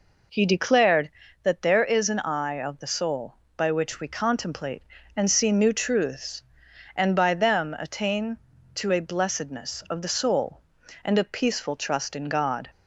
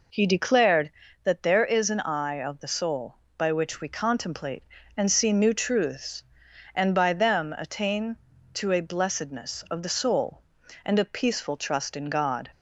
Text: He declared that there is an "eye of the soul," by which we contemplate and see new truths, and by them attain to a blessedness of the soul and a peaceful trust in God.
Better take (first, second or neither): neither